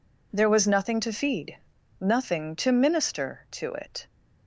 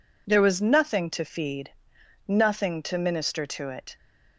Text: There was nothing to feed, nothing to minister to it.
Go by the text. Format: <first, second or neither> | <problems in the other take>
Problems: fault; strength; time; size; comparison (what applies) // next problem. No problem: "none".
neither | none